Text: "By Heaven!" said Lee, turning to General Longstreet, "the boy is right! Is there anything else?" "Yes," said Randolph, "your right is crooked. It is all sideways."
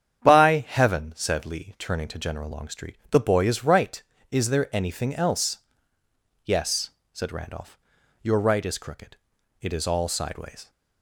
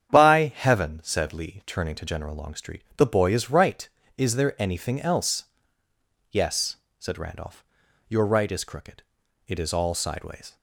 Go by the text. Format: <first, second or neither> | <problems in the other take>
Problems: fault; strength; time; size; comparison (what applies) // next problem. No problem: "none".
neither | starts louder than the rest; strong; the same in both